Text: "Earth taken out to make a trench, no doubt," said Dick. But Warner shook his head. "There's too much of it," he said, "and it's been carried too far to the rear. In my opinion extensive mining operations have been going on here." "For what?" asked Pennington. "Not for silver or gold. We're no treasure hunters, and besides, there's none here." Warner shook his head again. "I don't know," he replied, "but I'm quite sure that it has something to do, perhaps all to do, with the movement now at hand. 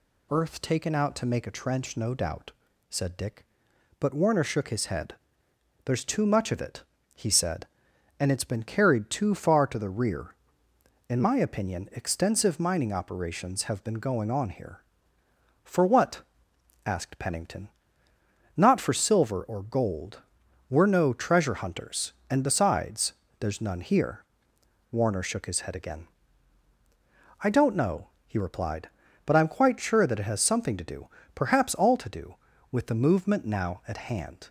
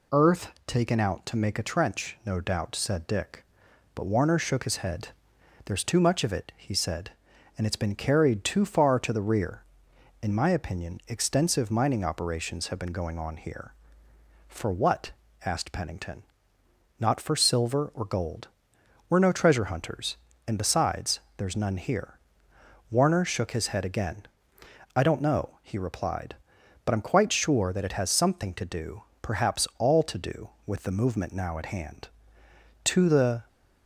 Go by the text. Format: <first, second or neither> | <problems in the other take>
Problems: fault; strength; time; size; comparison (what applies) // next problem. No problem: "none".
first | goes on to say "To the"; noticeable; from 32.8 s on; 0.62 s long